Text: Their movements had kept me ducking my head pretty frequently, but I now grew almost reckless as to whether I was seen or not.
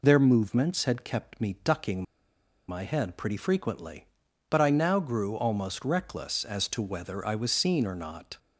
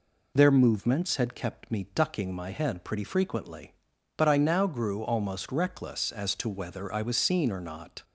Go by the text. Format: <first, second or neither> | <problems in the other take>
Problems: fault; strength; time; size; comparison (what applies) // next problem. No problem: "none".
second | pauses between "ducking" and "my"; noticeable; at 2.0 s; 0.65 s long